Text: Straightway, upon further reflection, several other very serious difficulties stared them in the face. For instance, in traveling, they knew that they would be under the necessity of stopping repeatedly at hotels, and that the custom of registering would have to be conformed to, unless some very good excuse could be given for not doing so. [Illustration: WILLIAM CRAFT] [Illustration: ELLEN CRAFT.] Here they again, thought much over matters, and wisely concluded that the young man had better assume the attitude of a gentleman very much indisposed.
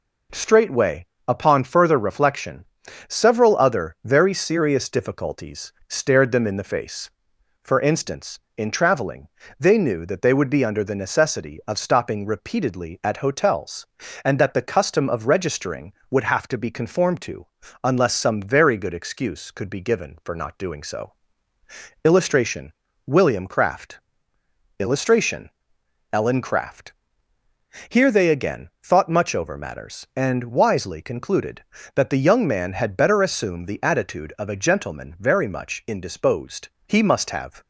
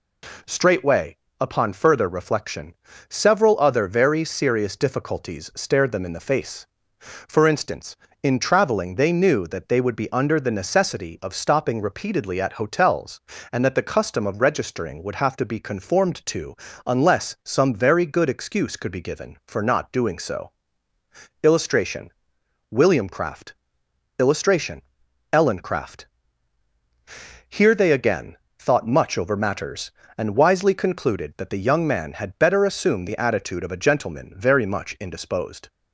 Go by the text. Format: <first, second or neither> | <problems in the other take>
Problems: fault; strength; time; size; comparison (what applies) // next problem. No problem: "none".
second | pauses between "difficulties" and "stared"; slight; at 5.7 s; 0.16 s long // pauses between "CRAFT" and "Illustration"; noticeable; at 23.9 s; 0.80 s long; noticeable in the second // goes on to say "He must have"; noticeable; from 36.8 s on; 0.74 s long